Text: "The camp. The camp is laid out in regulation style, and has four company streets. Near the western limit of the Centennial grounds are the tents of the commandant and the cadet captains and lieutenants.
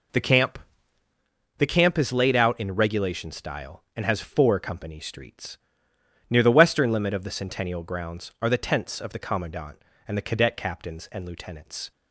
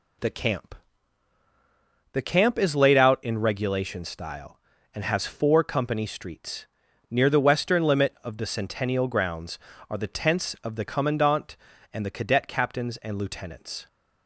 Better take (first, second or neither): neither